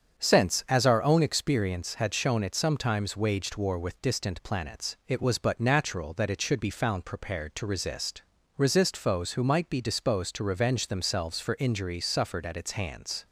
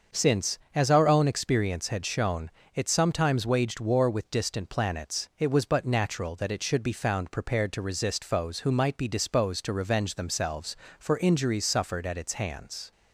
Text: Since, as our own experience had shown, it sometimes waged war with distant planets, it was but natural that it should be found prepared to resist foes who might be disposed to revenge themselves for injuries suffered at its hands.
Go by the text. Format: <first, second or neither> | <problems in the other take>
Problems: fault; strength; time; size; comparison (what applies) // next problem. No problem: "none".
second | starts louder than the rest; strong; until 1.2 s; 7.5 dB; also in the second // says "resist" twice; at 8.5 s